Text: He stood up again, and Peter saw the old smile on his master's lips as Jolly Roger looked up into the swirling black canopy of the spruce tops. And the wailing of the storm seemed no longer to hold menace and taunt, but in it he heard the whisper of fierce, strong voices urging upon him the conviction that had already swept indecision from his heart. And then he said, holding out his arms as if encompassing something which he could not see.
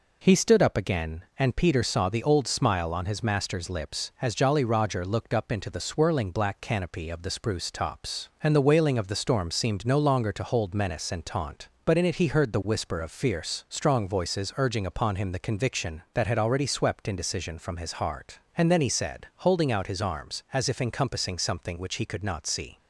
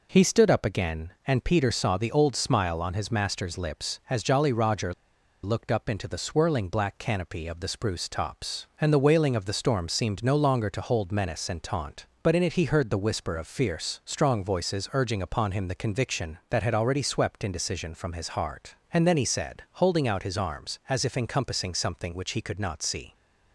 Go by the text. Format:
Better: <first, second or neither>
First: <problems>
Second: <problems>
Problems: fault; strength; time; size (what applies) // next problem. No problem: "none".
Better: first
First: none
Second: pauses between "Roger" and "looked"; noticeable; at 4.9 s; 0.50 s long